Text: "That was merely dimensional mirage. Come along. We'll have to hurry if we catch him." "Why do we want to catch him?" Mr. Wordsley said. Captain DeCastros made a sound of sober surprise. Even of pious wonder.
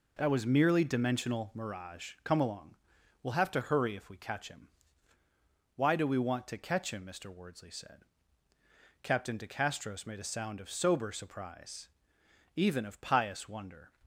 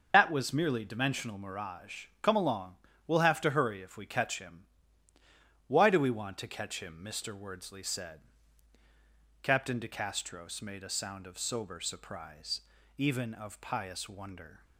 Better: first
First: none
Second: loses the start of "That"; at 0.1 s; 85 ms // starts louder than the rest; noticeable; until 1.1 s; 6 dB

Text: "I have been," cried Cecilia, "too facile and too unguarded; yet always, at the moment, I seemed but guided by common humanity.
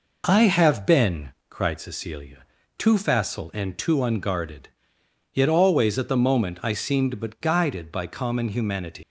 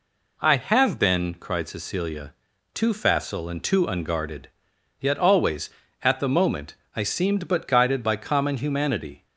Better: second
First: leaves "humanity" unfinished; at 9.0 s; 160 ms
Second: none

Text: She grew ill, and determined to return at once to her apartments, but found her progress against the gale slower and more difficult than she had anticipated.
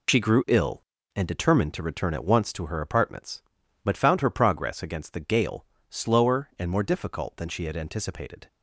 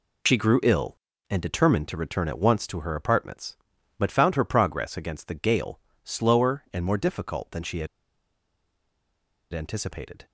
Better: first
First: pauses between "gale" and "slower"; slight; at 5.6 s; 0.24 s long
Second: pauses between "gale" and "slower"; slight; at 5.7 s; 0.24 s long // pauses between "had" and "anticipated"; strong; at 7.8 s; 1.6 s long

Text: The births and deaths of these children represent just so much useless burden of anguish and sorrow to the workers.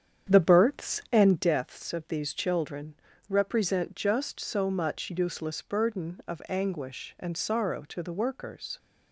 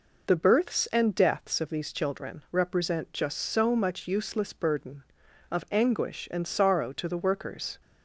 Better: second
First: starts louder than the rest; strong; until 1.5 s; 8.5 dB // pauses between "children" and "represent"; slight; at 2.9 s; 0.34 s long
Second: none

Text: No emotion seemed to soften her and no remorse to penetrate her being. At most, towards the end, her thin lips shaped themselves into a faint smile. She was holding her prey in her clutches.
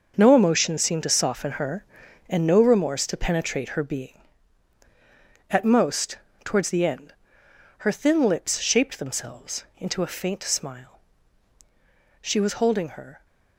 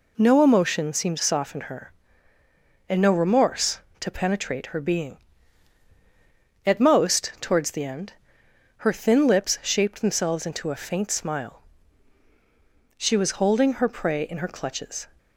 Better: second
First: starts louder than the rest; until 1.1 s; 6.5 dB // stops before "prey in her clutches"; at 13.2 s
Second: none

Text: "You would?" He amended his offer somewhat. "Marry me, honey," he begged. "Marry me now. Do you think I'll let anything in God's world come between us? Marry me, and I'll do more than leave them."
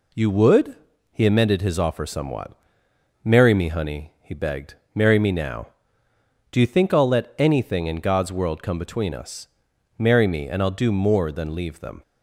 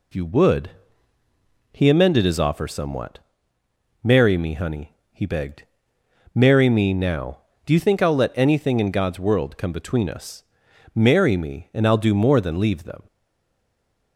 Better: first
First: none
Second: stays silent after the last word; from 13.0 s on; 1.1 s long

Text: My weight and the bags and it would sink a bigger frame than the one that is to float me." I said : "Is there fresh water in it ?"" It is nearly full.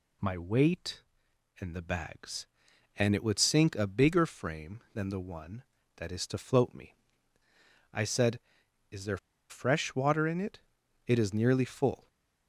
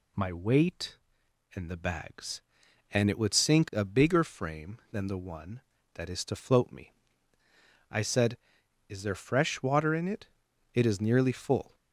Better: second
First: pauses between "there" and "fresh"; slight; at 9.1 s; 0.32 s long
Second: none

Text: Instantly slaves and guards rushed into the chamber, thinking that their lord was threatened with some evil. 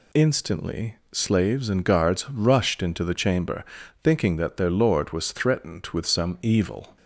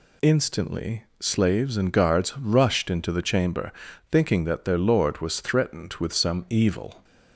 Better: neither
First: pauses between "Instantly" and "slaves"; slight; at 0.9 s; 0.16 s long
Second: pauses between "Instantly" and "slaves"; slight; at 1.0 s; 0.16 s long

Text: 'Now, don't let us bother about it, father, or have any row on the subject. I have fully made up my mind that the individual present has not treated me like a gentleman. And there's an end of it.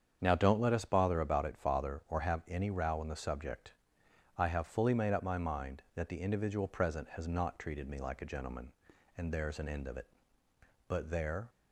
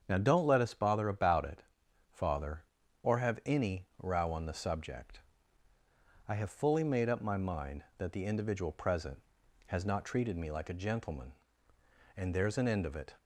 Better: second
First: starts louder than the rest; strong; until 1.2 s; 7.5 dB // goes on to say "But there"; noticeable; from 10.8 s on; 0.62 s long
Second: starts louder than the rest; strong; until 1.0 s; 7 dB

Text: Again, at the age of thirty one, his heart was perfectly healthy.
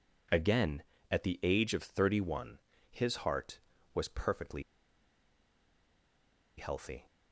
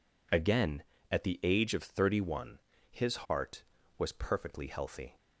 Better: second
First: pauses between "perfectly" and "healthy"; strong; at 4.6 s; 1.9 s long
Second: none

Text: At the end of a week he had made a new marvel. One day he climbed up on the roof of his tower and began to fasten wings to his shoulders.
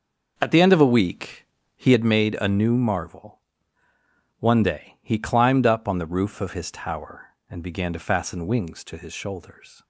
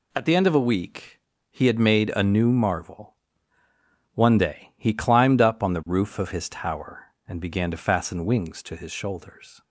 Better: second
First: starts louder than the rest; noticeable; until 2.1 s; 6 dB // pauses between "week" and "he"; slight; at 1.4 s; 0.30 s long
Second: pauses between "week" and "he"; slight; at 1.2 s; 0.30 s long

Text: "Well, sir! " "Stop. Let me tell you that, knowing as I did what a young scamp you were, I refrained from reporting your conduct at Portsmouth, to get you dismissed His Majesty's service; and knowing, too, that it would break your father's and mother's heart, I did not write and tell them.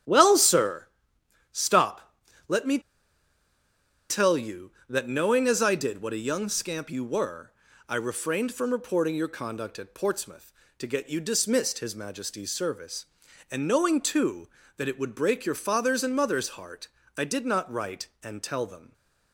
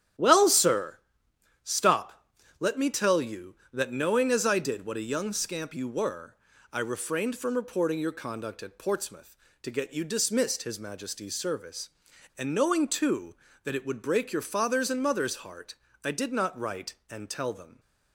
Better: second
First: starts louder than the rest; strong; until 1.3 s; 9 dB // pauses between "me" and "tell"; strong; at 2.7 s; 1.3 s long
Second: starts louder than the rest; strong; until 1.5 s; 9 dB

